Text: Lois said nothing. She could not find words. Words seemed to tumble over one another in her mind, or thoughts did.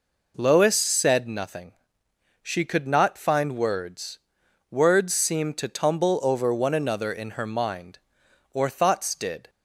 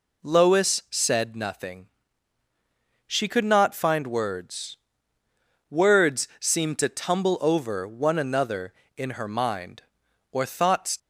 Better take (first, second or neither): first